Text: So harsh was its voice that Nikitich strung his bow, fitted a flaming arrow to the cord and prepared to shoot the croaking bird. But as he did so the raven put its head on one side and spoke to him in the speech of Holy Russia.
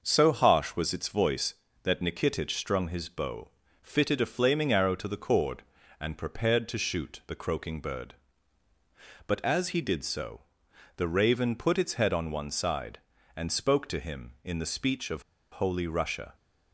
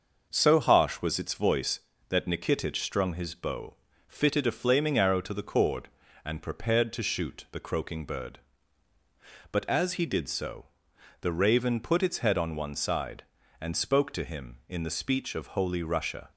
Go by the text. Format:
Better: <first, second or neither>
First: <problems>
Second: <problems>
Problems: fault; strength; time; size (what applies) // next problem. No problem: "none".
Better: second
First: starts louder than the rest; noticeable; until 1.0 s; 6 dB // pauses between "so" and "the"; noticeable; at 10.4 s; 0.56 s long // pauses between "of" and "Holy"; slight; at 15.2 s; 0.29 s long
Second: starts louder than the rest; until 1.3 s; 6 dB // pauses between "so" and "the"; noticeable; at 10.6 s; 0.56 s long